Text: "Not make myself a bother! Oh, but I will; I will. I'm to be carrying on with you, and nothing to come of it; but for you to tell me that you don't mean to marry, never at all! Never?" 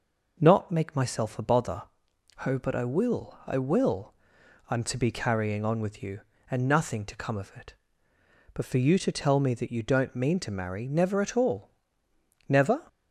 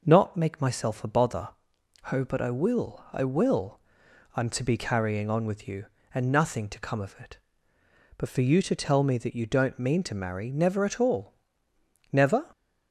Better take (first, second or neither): neither